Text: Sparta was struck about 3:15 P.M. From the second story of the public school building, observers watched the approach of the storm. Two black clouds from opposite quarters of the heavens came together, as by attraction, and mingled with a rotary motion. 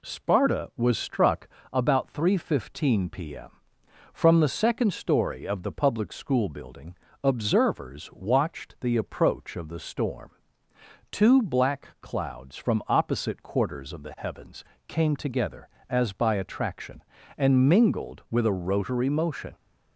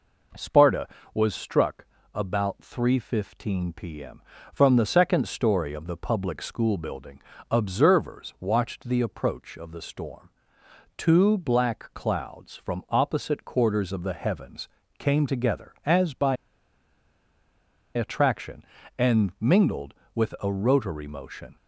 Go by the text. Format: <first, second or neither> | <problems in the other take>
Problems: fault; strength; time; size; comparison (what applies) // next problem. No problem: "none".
first | pauses between "struck" and "about"; slight; at 1.8 s; 0.30 s long; slight in the first // pauses between "heavens" and "came"; slight; at 14.6 s; 0.30 s long; slight in the first // pauses between "by" and "attraction"; strong; at 16.3 s; 1.5 s long